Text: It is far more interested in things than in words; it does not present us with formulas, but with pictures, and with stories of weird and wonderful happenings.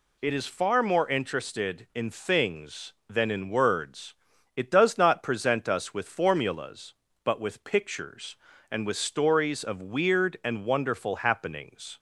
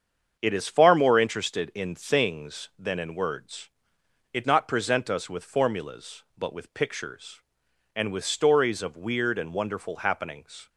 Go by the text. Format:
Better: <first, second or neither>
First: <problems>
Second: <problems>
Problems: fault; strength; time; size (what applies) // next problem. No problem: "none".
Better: first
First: none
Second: starts louder than the rest; strong; until 1.4 s; 7.5 dB // skips "does"; at 4.4 s